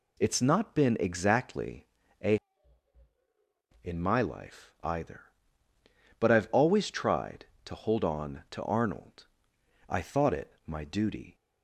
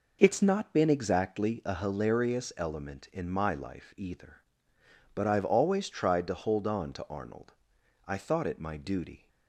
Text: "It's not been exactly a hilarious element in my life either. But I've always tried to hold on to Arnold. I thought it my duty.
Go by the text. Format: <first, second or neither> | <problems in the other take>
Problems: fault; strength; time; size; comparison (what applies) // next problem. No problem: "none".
second | pauses between "exactly" and "a"; at 1.8 s; 0.38 s long // skips "hilarious element"; at 3.1 s